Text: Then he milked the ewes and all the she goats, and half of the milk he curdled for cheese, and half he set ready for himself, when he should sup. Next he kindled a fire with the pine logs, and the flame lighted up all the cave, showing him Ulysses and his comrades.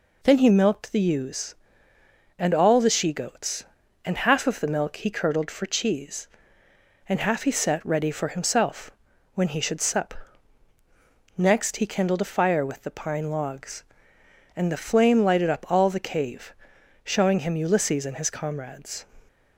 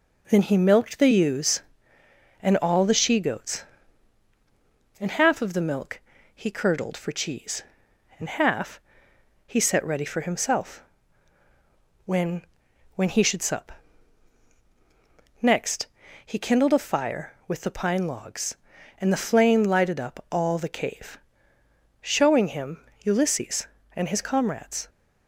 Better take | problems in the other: first | pauses between "milk" and "he"; slight; at 5.9 s; 0.34 s long // pauses between "half" and "he"; noticeable; at 8.7 s; 0.68 s long // says "when" twice; at 12.9 s // pauses between "Next" and "he"; slight; at 15.8 s; 0.36 s long // pauses between "him" and "Ulysses"; slight; at 22.7 s; 0.26 s long

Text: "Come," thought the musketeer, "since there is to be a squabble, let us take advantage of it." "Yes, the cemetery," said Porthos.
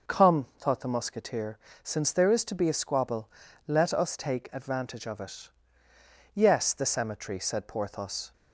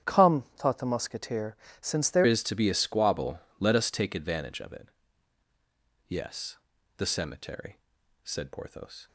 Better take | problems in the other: first | starts louder than the rest; strong; until 1.1 s; 9.5 dB // changes voice at "is"; from 2.2 s on; 6.8 s long

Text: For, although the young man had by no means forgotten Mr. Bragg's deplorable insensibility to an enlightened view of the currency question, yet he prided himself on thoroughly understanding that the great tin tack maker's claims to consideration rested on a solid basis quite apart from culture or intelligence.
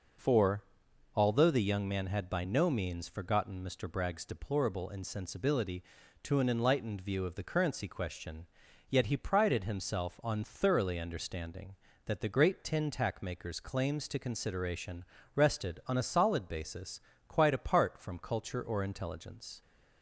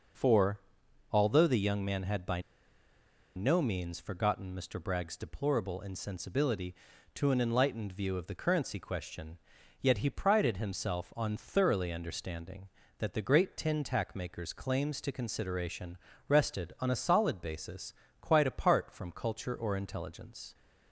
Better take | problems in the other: first | pauses between "by" and "no"; noticeable; at 2.3 s; 0.95 s long // pauses between "consideration" and "rested"; slight; at 15.9 s; 0.30 s long; slight in the first // pauses between "basis" and "quite"; slight; at 17.9 s; 0.28 s long; slight in the first

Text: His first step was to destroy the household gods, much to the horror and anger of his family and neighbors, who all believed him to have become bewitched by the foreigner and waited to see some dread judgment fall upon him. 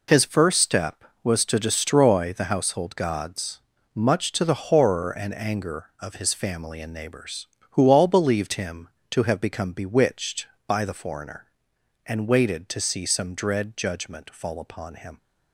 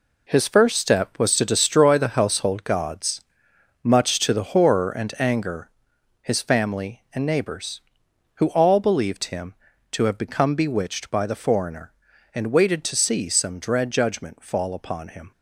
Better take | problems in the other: first | skips "of"; at 5.9 s

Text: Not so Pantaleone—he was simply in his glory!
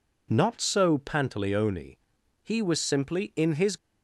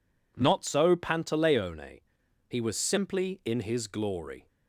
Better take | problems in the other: second | stops before "glory"; at 3.7 s

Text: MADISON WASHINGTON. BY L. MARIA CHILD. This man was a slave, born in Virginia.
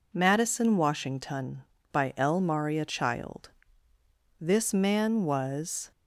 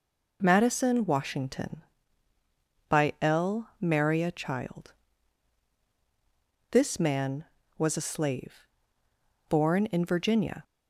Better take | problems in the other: second | stops before "a slave born in Virginia"; at 5.9 s

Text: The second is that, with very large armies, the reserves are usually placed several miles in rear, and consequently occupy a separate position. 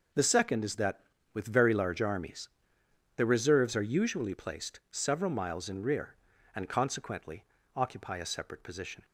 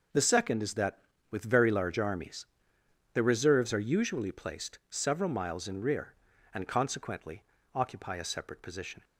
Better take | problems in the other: neither | pauses between "consequently" and "occupy"; slight; the same in both

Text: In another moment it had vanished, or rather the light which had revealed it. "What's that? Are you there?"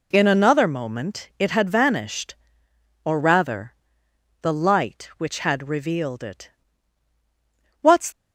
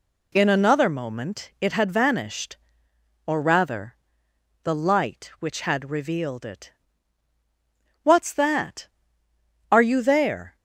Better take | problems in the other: second | pauses between "rather" and "the"; noticeable; at 3.7 s; 0.68 s long; noticeable in the second // stops before "that Are you there"; at 8.1 s

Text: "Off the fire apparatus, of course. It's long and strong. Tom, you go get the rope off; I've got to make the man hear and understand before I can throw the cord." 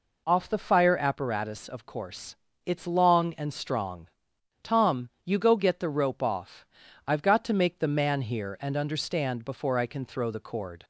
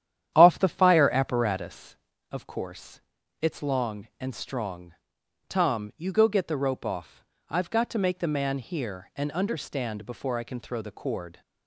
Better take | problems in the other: first | starts louder than the rest; strong; until 1.8 s; 10.5 dB

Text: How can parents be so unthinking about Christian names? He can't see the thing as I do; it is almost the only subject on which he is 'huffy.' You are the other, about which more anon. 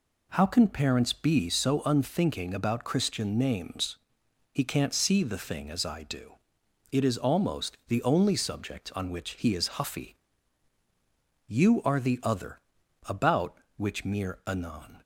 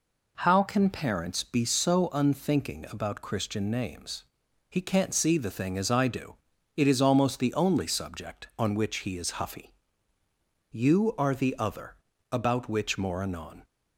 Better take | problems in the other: second | says "mere" for "more"; at 14.0 s

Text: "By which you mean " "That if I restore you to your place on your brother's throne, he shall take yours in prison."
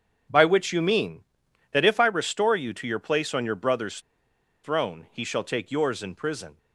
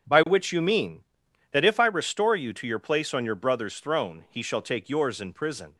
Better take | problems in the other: second | starts louder than the rest; until 1.5 s; 6.5 dB; also in the second // pauses between "brother's" and "throne"; noticeable; at 3.9 s; 0.64 s long

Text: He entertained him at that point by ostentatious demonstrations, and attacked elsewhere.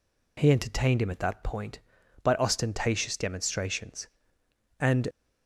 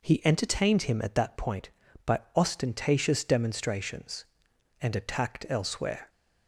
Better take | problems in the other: second | stops before "attacked elsewhere"; at 5.1 s

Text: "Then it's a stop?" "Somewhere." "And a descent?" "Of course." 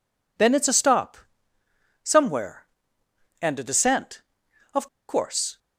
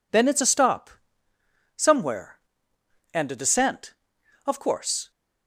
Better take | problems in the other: second | pauses between "Of" and "course"; slight; at 4.8 s; 0.20 s long

